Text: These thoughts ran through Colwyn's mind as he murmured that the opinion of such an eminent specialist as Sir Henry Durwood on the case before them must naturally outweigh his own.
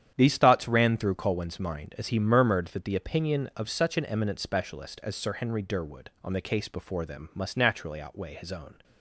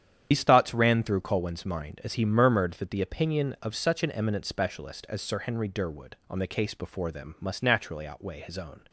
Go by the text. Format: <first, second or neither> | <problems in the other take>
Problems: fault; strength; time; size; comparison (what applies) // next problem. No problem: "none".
first | loses the start of "These"; at 0.3 s; 100 ms // starts louder than the rest; strong; until 1.3 s; 9 dB; strong in the first